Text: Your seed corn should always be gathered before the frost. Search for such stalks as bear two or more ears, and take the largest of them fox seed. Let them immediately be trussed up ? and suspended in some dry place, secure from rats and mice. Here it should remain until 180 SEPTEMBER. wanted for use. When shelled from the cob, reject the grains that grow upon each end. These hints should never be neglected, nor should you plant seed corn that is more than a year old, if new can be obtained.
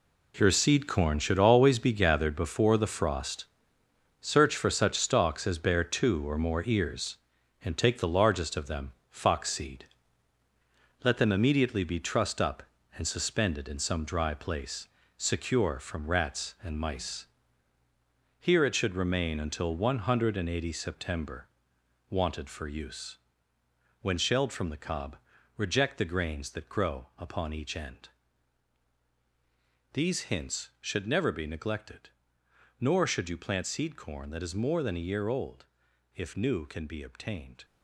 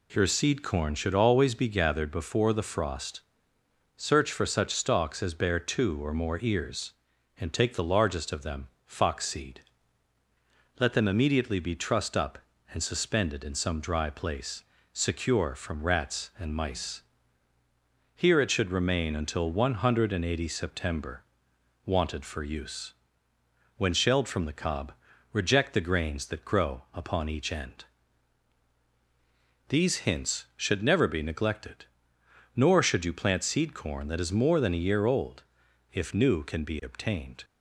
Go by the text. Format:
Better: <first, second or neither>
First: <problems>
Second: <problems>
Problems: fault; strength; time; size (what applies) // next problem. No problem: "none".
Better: second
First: gets quieter; strong; throughout; 10.5 dB // pauses between "them" and "fox"; slight; at 8.9 s; 0.18 s long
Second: pauses between "them" and "fox"; slight; at 8.6 s; 0.18 s long